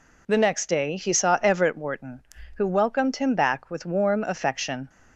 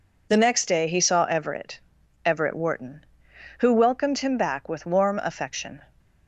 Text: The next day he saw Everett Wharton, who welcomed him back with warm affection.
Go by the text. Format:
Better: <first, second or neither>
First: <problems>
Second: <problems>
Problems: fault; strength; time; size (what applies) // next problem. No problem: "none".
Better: first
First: none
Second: says "Everett" twice; at 2.2 s